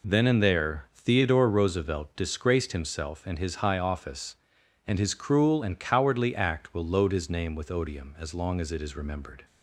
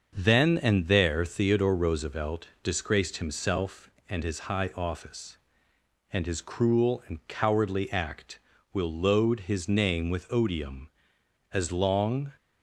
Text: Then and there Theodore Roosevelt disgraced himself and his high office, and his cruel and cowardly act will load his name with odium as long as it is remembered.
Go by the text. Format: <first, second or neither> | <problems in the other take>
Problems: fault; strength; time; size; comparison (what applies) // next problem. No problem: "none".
first | starts louder than the rest; until 1.1 s; 6.5 dB // stops before "as it is remembered"; at 12.3 s